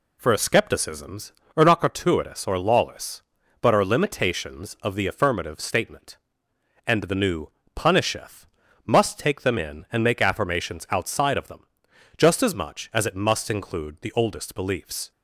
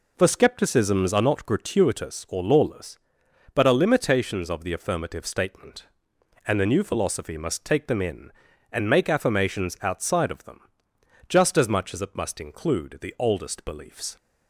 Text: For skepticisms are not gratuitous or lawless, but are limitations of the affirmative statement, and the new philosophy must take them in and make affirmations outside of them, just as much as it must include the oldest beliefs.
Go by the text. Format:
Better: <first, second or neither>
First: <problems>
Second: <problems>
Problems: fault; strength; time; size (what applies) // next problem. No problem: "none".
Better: second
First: says "punisheth" for "philosophy"; at 7.7 s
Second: none